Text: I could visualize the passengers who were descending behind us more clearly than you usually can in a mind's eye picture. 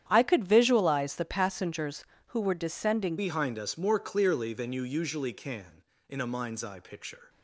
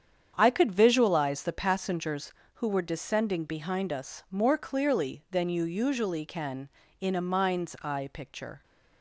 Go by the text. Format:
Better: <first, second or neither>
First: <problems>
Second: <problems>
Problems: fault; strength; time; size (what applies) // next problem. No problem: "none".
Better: second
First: starts louder than the rest; strong; until 1.0 s; 9.5 dB // changes voice at "behind"; from 3.1 s on; 4.1 s long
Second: starts louder than the rest; strong; until 1.3 s; 8 dB